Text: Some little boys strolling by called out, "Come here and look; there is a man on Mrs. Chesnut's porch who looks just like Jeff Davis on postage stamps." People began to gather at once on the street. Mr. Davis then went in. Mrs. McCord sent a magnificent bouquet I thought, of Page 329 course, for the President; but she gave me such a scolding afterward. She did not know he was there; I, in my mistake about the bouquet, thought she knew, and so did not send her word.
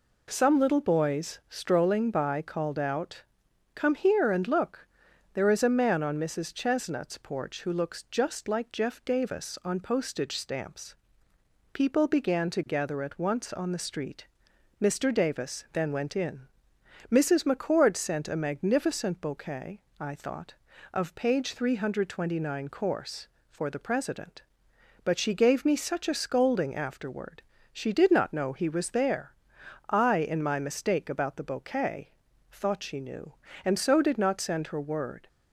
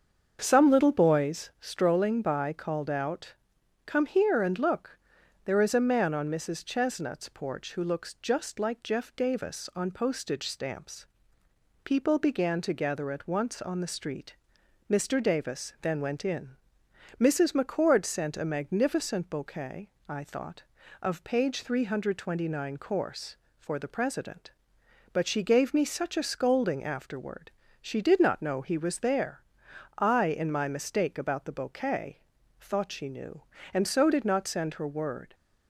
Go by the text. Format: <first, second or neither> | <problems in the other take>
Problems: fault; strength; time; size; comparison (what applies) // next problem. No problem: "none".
first | starts louder than the rest; until 1.3 s; 7 dB // pauses between "bouquet" and "I"; slight; at 19.8 s; 0.18 s long; slight in the first